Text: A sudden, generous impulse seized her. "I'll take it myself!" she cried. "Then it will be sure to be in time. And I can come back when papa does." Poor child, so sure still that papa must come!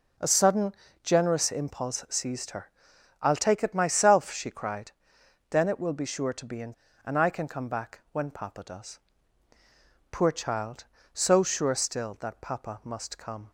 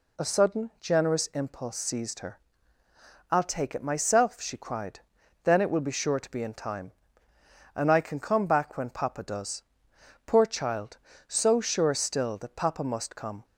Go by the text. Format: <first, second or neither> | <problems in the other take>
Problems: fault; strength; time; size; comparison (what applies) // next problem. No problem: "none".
second | skips "time"; at 6.8 s